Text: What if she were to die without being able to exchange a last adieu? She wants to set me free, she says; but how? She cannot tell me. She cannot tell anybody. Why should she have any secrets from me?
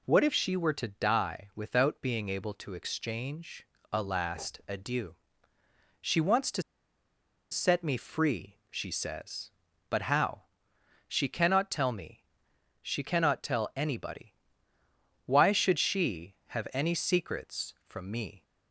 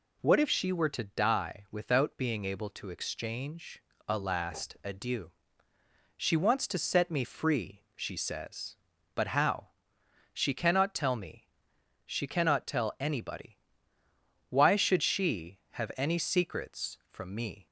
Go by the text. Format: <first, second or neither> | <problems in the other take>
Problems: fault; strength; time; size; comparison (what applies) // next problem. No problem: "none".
second | pauses between "exchange" and "a"; slight; at 3.6 s; 0.24 s long; slight in the second // pauses between "to" and "set"; noticeable; at 6.6 s; 0.89 s long